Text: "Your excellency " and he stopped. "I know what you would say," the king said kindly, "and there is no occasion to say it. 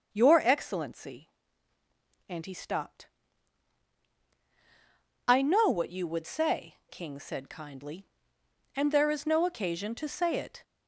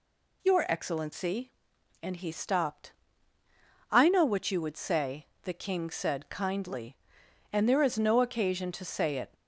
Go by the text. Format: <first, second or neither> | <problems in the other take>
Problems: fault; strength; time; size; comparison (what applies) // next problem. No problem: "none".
second | starts louder than the rest; until 1.1 s; 6.5 dB // skips "the"; at 6.8 s